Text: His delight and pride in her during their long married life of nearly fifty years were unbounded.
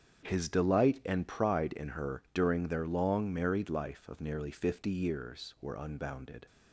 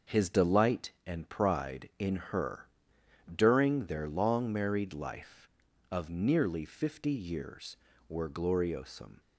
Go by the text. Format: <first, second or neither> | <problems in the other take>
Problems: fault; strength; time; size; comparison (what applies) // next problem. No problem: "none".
first | starts louder than the rest; until 1.2 s; 6.5 dB; strong in the first // pauses between "her" and "during"; noticeable; at 2.6 s; 0.66 s long // says "gloriosum" for "unbounded"; at 8.2 s